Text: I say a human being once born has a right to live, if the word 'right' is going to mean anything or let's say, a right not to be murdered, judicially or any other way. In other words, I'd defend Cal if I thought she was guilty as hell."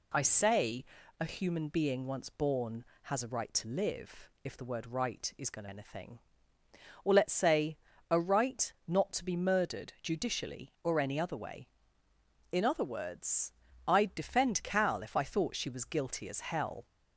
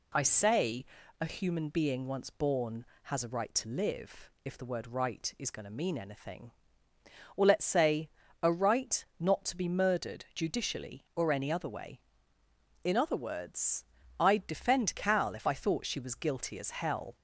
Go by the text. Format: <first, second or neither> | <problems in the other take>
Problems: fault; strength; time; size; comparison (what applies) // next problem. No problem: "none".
second | pauses between "say" and "a"; slight; at 0.8 s; 0.34 s long; slight in the second // skips "mean"; at 5.6 s